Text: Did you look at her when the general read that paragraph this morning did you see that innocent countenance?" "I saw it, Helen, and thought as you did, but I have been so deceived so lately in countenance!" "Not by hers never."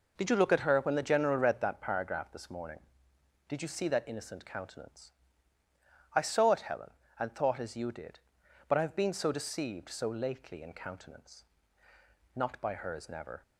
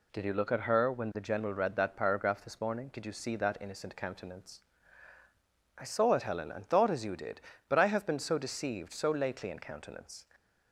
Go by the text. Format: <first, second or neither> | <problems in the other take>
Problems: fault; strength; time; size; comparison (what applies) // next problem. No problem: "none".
first | stops before "Not by hers never"; at 10.3 s